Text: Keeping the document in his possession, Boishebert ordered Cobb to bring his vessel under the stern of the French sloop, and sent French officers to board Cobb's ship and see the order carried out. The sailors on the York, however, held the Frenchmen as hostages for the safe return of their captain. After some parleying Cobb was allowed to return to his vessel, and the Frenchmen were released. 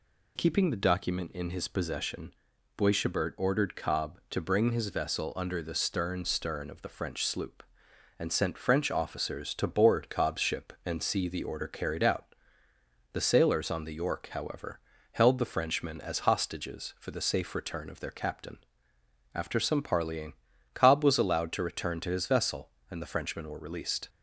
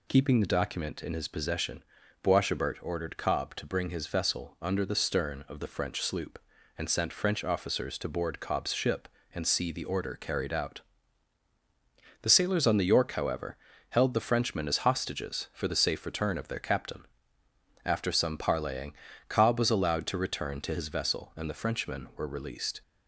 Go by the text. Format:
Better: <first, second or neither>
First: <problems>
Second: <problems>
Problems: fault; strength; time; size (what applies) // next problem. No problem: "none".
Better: second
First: says "stern" twice; at 6.2 s // pauses between "parleying" and "Cobb"; at 20.3 s; 0.40 s long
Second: pauses between "parleying" and "Cobb"; slight; at 18.9 s; 0.36 s long